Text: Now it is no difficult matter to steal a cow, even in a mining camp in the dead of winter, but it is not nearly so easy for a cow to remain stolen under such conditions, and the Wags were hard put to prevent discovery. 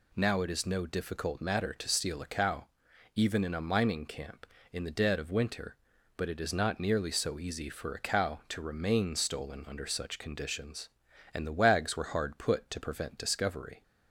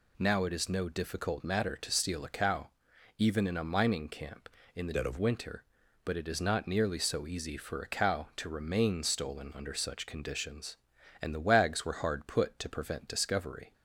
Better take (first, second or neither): first